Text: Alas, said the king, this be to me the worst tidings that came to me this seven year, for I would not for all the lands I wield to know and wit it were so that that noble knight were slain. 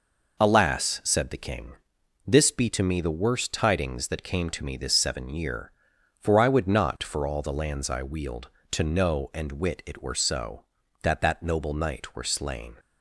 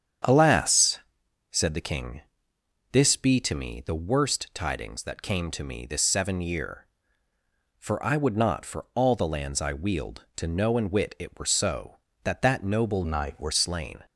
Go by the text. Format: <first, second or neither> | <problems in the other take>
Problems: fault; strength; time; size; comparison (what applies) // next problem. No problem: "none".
first | starts louder than the rest; strong; until 1.7 s; 8.5 dB // changes voice from "knight" to "were"; from 13.0 to 13.5 s; 0.5 s long